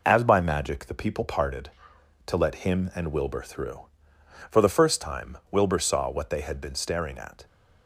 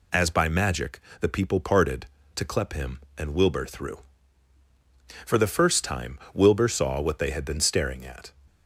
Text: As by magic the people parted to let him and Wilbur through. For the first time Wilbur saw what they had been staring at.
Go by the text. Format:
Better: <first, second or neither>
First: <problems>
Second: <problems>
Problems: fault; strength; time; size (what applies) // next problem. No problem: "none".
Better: first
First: none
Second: pauses between "magic" and "the"; slight; at 0.9 s; 0.22 s long // says "clep" for "let"; at 2.4 s